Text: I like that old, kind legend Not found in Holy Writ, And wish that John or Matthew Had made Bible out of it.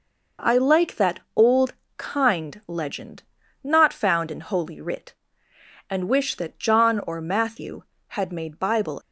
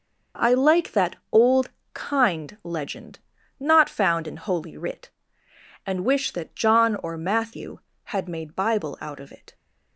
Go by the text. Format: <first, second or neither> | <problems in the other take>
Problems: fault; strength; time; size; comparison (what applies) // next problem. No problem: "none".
second | pauses between "that" and "old"; slight; at 1.1 s; 0.16 s long; slight in the second // pauses between "legend" and "Not"; at 3.2 s; 0.38 s long; also in the second // stops before "out of it"; at 9.0 s